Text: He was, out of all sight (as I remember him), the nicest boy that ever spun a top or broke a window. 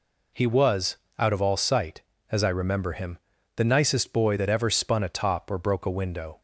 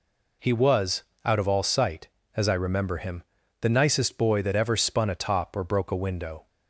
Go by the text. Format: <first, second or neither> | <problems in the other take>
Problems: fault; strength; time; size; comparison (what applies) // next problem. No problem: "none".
neither | none